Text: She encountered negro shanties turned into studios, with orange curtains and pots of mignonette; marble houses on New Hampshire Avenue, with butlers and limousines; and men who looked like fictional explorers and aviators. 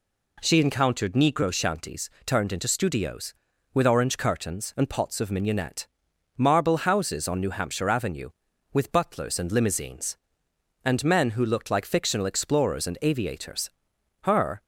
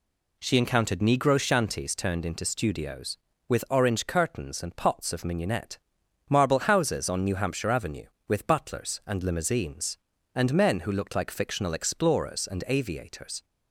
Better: second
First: pauses between "shanties" and "turned"; slight; at 2.0 s; 0.16 s long // goes on to say "Her"; slight; from 14.2 s on; 0.42 s long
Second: none

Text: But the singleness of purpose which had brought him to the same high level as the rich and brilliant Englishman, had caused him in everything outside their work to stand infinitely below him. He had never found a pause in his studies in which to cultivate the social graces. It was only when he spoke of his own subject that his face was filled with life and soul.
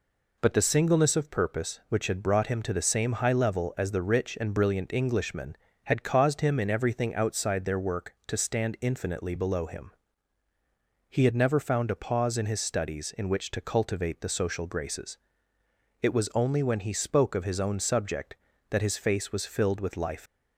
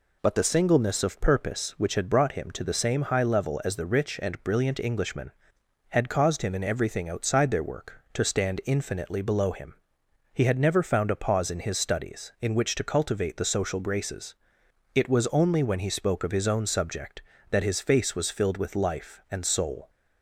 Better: second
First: stops before "and soul"; at 20.2 s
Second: none

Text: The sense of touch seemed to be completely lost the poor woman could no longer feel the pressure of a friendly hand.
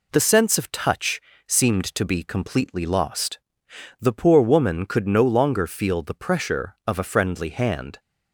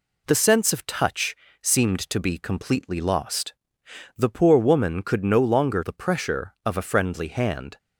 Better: first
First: pauses between "touch" and "seemed"; slight; at 1.2 s; 0.26 s long // pauses between "lost" and "the"; noticeable; at 3.3 s; 0.62 s long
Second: pauses between "touch" and "seemed"; slight; at 1.3 s; 0.26 s long // pauses between "lost" and "the"; noticeable; at 3.5 s; 0.64 s long // skips "feel"; at 5.8 s

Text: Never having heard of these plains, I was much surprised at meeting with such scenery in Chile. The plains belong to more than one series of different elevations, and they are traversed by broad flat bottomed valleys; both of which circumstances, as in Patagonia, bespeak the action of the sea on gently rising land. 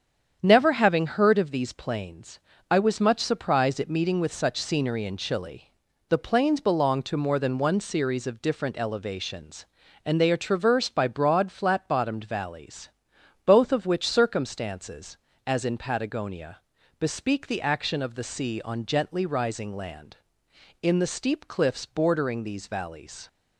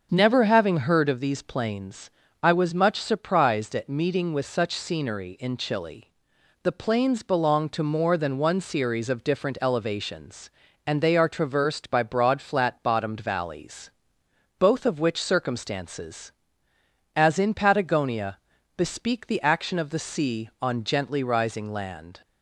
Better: second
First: starts louder than the rest; strong; until 1.4 s; 8 dB // goes on to say "In the steep cliffs bordering these valleys"; strong; from 20.8 s on; 2.4 s long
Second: starts louder than the rest; until 1.1 s; 7 dB

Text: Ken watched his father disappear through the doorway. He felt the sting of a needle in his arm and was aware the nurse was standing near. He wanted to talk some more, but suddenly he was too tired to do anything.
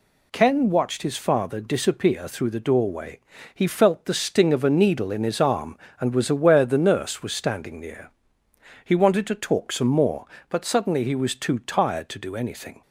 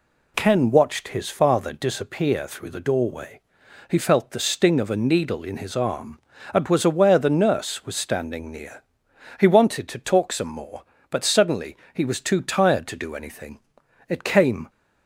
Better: first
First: none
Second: pauses between "suddenly" and "he"; slight; at 11.7 s; 0.16 s long // goes on to say "It came"; from 14.0 s on; 0.60 s long

